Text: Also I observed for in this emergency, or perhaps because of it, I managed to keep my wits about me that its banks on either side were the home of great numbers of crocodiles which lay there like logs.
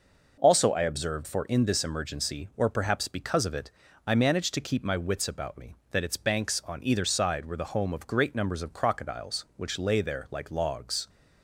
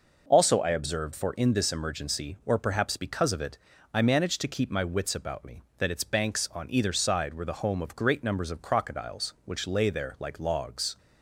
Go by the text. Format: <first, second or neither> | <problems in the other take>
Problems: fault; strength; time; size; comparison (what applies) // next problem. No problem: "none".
neither | none